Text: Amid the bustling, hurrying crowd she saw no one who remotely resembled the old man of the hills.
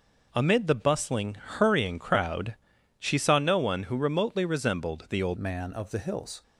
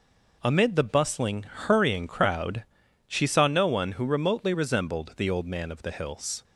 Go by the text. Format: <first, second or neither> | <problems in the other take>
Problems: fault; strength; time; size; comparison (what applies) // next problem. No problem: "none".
second | pauses between "crowd" and "she"; noticeable; at 2.5 s; 0.46 s long; noticeable in the second // changes voice at "man"; from 5.3 s on; 1.1 s long